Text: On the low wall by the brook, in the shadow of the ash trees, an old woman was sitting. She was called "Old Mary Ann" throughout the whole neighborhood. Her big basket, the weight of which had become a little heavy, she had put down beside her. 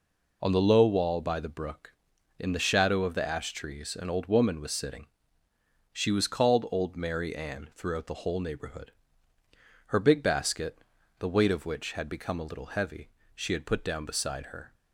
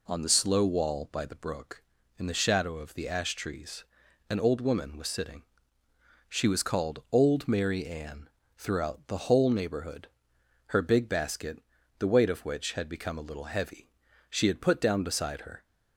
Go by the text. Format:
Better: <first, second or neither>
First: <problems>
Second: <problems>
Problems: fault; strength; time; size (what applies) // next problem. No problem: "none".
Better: first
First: none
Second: says "slow" for "low"; at 0.2 s // pauses between "Ann" and "throughout"; slight; at 8.2 s; 0.26 s long